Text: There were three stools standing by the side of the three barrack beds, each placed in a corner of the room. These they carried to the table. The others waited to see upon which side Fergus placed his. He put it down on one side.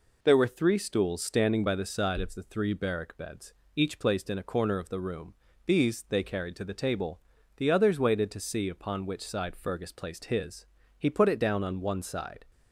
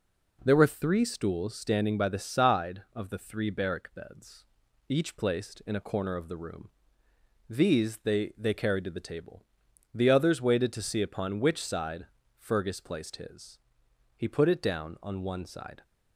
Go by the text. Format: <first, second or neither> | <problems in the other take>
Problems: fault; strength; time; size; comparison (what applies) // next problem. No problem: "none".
first | says "they" twice; at 8.3 s // pauses between "side" and "Fergus"; slight; at 12.0 s; 0.32 s long